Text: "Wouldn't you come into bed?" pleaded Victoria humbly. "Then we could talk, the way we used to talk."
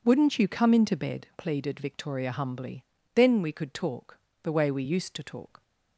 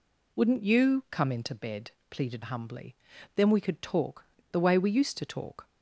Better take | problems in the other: first | skips "Victoria"; at 2.4 s

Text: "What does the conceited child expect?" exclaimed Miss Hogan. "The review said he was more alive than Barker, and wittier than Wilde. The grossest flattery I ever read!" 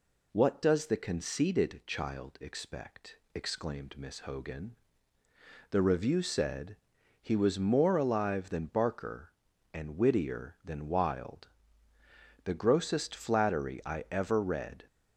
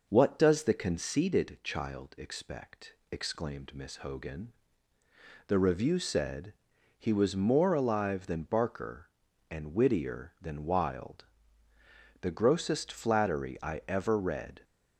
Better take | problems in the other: first | starts louder than the rest; noticeable; until 1.1 s; 5.5 dB // pauses between "said" and "he"; at 6.5 s; 0.44 s long; also in the first

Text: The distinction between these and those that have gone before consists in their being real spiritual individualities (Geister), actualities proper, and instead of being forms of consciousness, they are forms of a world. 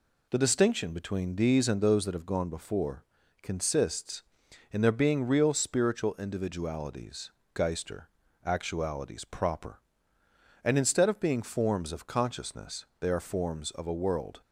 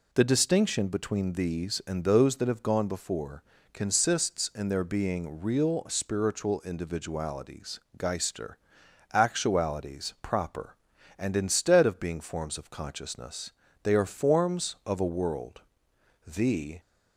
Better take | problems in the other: first | pauses between "before" and "consists"; slight; at 3.4 s; 0.30 s long; also in the first // goes on to say "The"; from 16.2 s on; 0.54 s long

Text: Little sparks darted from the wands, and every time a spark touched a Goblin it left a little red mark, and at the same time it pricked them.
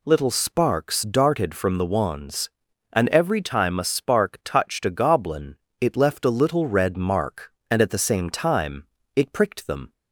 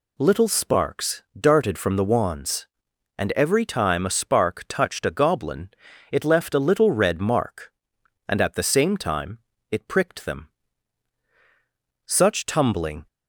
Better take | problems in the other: first | pauses between "sparks" and "darted"; slight; at 1.2 s; 0.18 s long // pauses between "Goblin" and "it"; at 5.6 s; 0.42 s long; slight in the first // pauses between "time" and "it"; slight; at 9.3 s; 0.34 s long; slight in the first // goes on to say "Such tumbling"; noticeable; from 12.0 s on; 1.0 s long

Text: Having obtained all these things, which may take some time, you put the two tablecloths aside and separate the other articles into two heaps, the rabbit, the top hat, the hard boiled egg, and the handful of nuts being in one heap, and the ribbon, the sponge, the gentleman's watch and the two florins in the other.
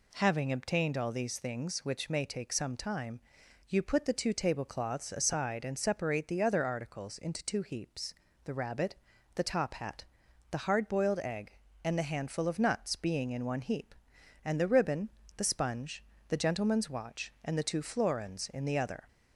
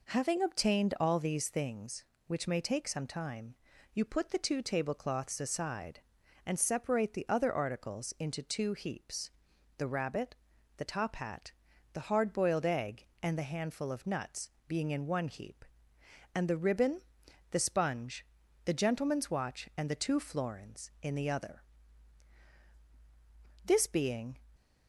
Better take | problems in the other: first | pauses between "nuts" and "being"; slight; at 14.5 s; 0.18 s long // goes on to say "This being"; noticeable; from 23.6 s on; 0.70 s long

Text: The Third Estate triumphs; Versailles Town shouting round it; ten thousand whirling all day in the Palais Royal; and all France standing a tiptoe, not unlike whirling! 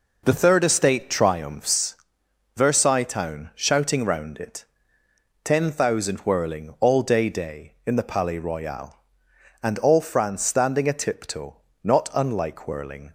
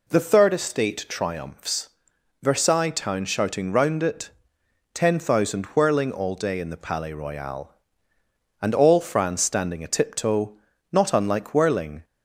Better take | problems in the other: second | says "day" twice; at 7.2 s

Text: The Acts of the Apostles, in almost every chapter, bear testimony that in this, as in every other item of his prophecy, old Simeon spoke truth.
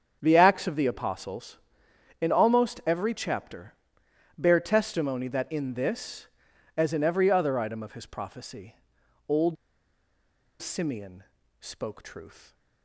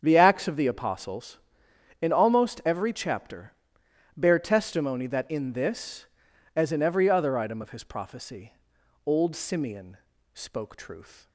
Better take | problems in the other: second | starts louder than the rest; strong; until 1.2 s; 8 dB; strong in the second // pauses between "old" and "Simeon"; at 9.5 s; 1.0 s long // pauses between "Simeon" and "spoke"; at 11.2 s; 0.38 s long; also in the second

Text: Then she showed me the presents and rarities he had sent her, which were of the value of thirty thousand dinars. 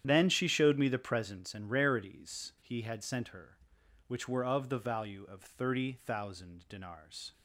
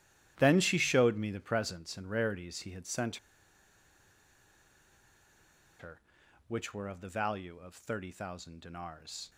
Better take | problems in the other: first | starts louder than the rest; strong; until 1.3 s; 12 dB; strong in the first // pauses between "sent" and "her"; strong; at 3.1 s; 2.6 s long

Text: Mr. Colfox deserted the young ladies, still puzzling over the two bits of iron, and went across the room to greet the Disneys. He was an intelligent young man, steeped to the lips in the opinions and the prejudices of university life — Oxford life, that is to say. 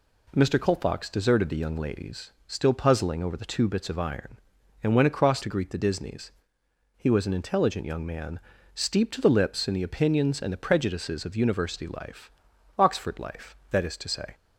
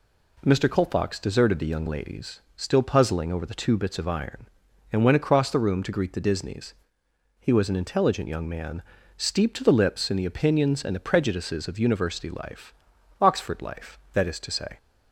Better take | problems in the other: second | skips "the room"; at 5.4 s

